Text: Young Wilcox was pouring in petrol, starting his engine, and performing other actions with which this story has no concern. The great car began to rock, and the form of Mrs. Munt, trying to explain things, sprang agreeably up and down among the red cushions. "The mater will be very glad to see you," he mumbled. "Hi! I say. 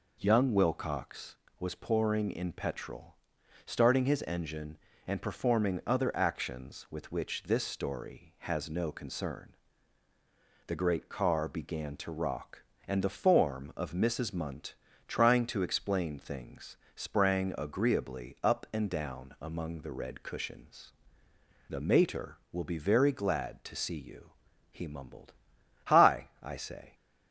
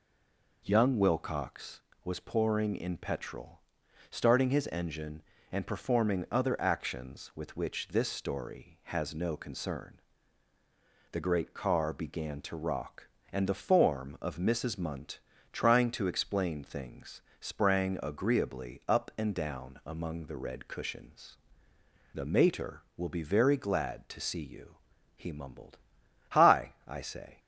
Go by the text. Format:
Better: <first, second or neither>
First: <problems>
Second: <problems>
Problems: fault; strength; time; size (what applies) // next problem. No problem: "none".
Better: first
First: none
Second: stays silent before the first word; slight; until 0.6 s; 0.6 s long